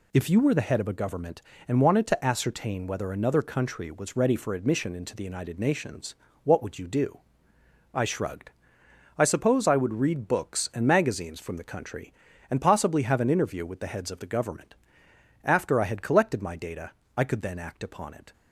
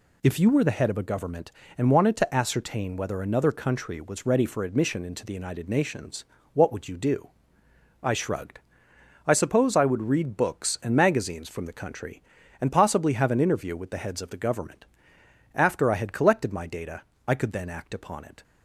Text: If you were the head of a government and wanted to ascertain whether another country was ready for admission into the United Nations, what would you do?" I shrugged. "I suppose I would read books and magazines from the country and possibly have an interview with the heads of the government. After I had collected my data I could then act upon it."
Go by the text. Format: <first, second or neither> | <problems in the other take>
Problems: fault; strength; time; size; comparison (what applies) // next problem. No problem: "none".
neither | pauses between "data" and "I"; slight; the same in both